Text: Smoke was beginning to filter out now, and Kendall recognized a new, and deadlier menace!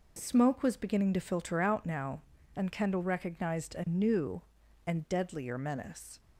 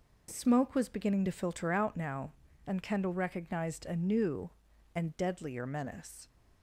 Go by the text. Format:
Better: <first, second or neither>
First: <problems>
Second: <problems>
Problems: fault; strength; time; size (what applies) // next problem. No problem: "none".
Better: neither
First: none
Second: none